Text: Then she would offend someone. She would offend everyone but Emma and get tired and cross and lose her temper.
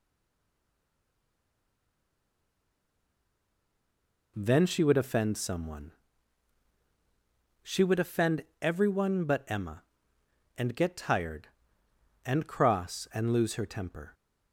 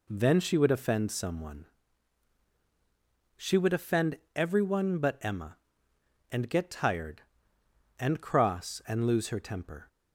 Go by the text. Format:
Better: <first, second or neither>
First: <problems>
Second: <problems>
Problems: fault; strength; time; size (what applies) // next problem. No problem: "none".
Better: second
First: stays silent before the first word; strong; until 4.3 s; 4.3 s long // pauses between "offend" and "everyone"; slight; at 8.4 s; 0.18 s long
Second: pauses between "offend" and "everyone"; slight; at 4.1 s; 0.18 s long